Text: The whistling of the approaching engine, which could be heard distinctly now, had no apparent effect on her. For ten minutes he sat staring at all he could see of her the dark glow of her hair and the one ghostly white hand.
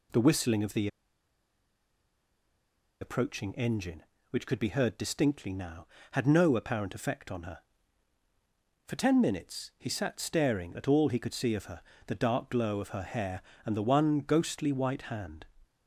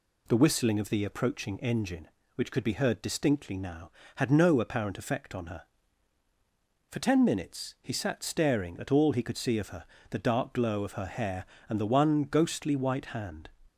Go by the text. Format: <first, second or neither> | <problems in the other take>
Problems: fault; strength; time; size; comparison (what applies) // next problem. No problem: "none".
second | pauses between "the" and "approaching"; strong; at 0.8 s; 2.1 s long // pauses between "her" and "the"; slight; at 11.8 s; 0.26 s long; slight in the second